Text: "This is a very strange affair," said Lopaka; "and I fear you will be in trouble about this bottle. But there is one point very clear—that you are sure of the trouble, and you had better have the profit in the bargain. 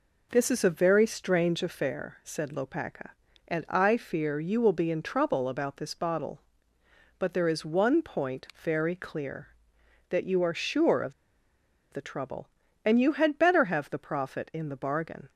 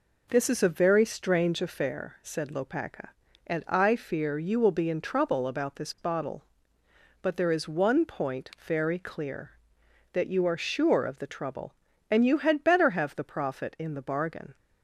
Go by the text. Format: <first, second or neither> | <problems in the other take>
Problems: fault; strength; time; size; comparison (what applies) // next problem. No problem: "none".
second | pauses between "of" and "the"; noticeable; at 11.1 s; 0.80 s long